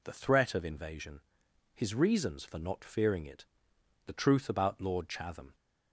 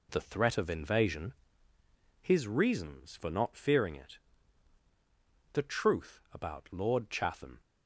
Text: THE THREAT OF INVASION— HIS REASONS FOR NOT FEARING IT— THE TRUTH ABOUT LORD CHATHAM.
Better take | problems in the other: neither | none

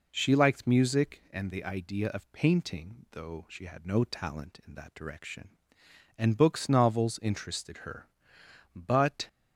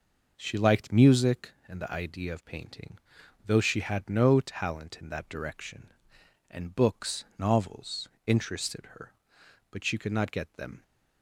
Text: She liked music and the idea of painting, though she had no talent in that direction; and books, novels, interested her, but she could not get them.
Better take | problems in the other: second | stops before "she could not get them"; at 9.2 s

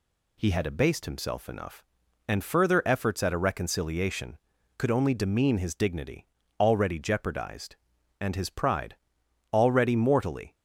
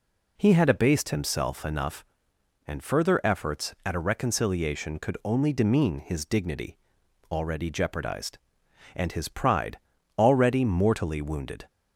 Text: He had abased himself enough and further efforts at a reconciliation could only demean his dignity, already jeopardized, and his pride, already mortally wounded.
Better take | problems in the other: second | stops before "wounded"; at 10.5 s

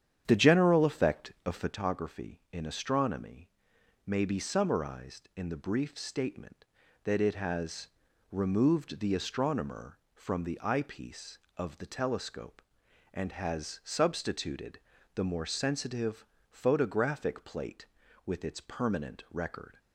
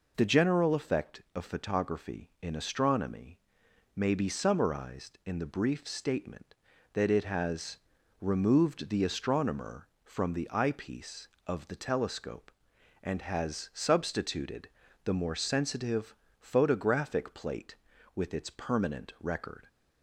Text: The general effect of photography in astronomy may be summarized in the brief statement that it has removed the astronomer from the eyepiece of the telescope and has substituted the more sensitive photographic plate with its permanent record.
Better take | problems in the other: second | starts louder than the rest; strong; until 1.8 s; 9 dB // pauses between "astronomy" and "may"; noticeable; at 3.4 s; 0.60 s long; noticeable in the second // pauses between "has" and "removed"; at 7.8 s; 0.44 s long; also in the second // pauses between "substituted" and "the"; slight; at 14.8 s; 0.34 s long; slight in the second // pauses between "sensitive" and "photographic"; slight; at 16.2 s; 0.26 s long; slight in the second

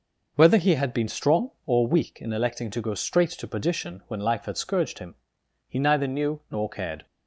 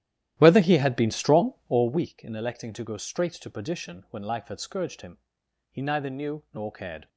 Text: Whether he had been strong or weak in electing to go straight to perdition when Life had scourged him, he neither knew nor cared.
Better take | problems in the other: first | starts louder than the rest; strong; until 2.1 s; 13 dB

